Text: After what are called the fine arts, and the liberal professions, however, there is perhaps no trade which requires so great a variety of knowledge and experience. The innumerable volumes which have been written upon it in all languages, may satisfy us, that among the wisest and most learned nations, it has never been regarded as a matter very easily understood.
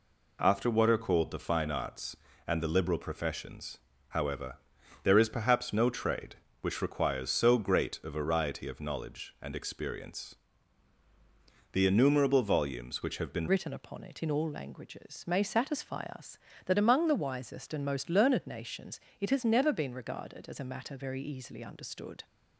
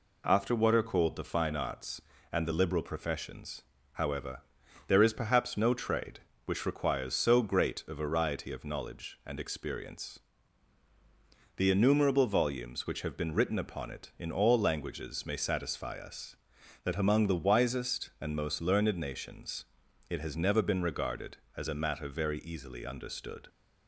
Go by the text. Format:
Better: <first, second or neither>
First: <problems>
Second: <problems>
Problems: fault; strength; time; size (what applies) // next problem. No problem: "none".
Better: second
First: changes voice at "written"; from 13.4 s on; 8.8 s long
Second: none